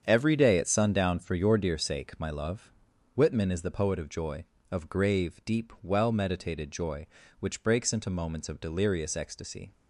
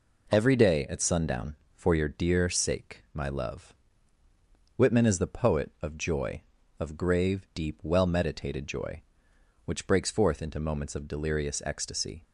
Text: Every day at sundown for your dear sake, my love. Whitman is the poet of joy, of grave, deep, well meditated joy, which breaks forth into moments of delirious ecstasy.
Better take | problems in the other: second | starts louder than the rest; strong; until 1.0 s; 7.5 dB // skips "forth"; at 7.9 s

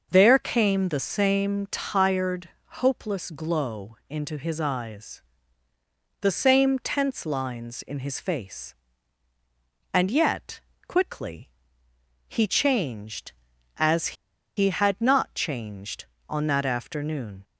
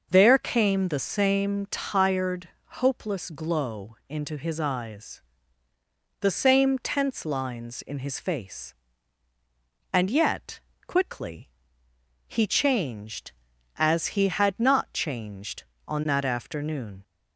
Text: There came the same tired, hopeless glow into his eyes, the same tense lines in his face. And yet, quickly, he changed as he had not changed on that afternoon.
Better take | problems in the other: second | starts louder than the rest; noticeable; until 1.1 s; 6 dB // pauses between "as" and "he"; at 14.1 s; 0.43 s long

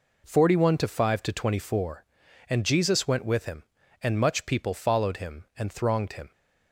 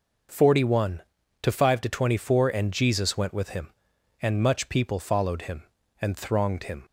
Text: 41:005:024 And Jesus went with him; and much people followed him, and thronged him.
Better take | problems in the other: neither | none

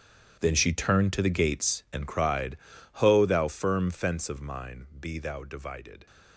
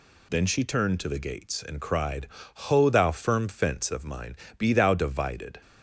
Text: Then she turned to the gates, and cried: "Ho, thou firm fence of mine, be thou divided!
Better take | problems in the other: second | gets quieter; strong; throughout; 15.5 dB

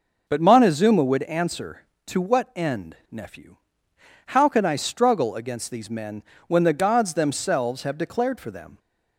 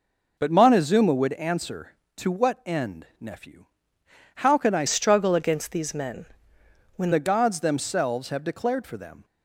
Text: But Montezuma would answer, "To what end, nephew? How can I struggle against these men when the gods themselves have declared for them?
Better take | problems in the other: first | changes voice from "struggle" to "when"; from 4.8 to 7.1 s; 2.3 s long // pauses between "men" and "when"; noticeable; at 6.2 s; 0.70 s long; slight in the first

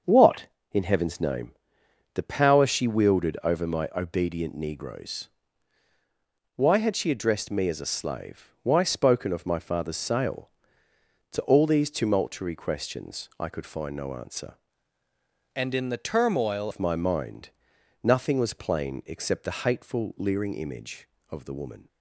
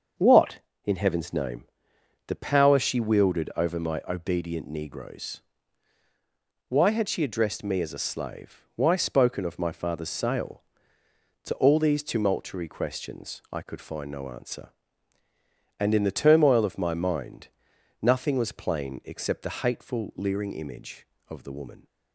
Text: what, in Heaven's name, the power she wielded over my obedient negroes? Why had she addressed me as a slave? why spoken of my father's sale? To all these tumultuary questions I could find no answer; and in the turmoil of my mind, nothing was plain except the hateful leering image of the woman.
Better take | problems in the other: second | starts louder than the rest; until 1.3 s; 6.5 dB; also in the second // changes voice from "and" to "turmoil"; from 15.5 to 16.7 s; 1.2 s long

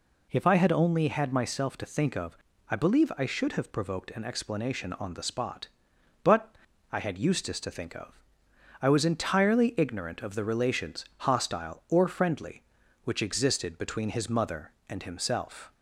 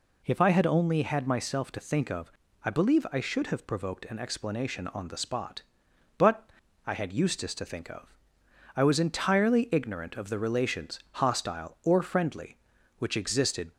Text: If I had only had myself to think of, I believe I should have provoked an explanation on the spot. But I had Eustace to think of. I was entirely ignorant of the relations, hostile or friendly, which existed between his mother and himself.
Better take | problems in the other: first | pauses between "But" and "I"; at 6.4 s; 0.38 s long; also in the first // stops before "between his mother and himself"; at 13.7 s

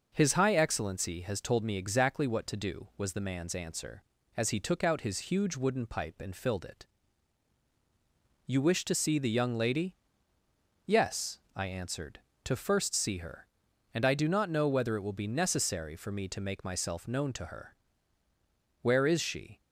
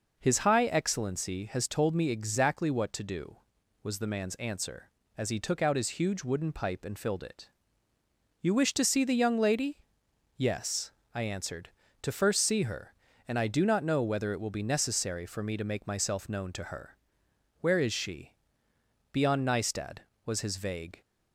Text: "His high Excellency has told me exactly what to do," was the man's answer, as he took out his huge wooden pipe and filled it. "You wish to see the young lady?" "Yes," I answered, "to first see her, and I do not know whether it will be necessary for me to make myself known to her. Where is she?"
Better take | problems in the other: first | goes on to say "Beyond Nystad was his vague"; strong; from 19.1 s on; 1.8 s long

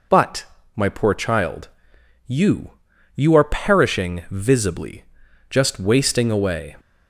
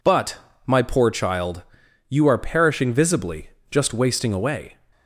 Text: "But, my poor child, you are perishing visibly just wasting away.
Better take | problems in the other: second | says "you" twice; at 3.1 s // pauses between "visibly" and "just"; at 5.0 s; 0.44 s long; slight in the second

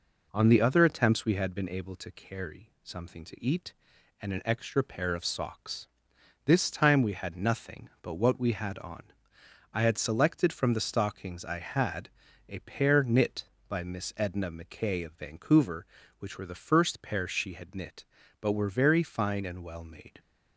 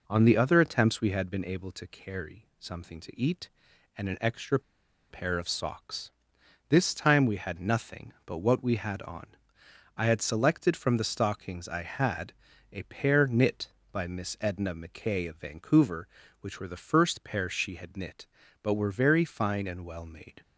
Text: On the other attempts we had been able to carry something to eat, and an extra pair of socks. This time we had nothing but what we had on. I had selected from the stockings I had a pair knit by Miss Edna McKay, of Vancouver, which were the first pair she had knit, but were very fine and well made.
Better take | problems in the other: first | pauses between "extra" and "pair"; noticeable; at 4.5 s; 0.50 s long // pauses between "had" and "a"; at 12.3 s; 0.38 s long; also in the first

